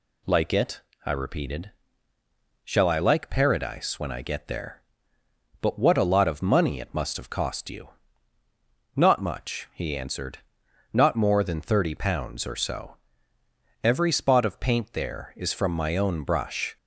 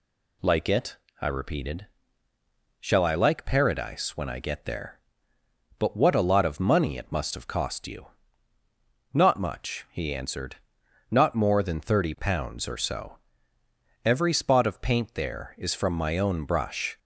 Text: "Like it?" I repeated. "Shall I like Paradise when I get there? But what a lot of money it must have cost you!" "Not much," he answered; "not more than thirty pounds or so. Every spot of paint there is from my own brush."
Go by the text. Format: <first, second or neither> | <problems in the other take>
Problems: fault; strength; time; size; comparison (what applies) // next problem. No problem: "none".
neither | none